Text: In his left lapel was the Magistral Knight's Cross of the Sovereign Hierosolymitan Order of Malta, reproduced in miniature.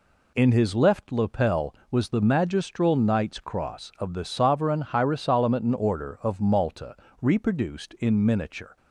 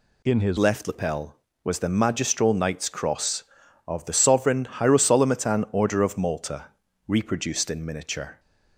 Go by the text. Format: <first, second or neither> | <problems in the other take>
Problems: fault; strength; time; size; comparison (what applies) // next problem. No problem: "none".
first | changes voice at "left"; from 0.5 s on; 7.8 s long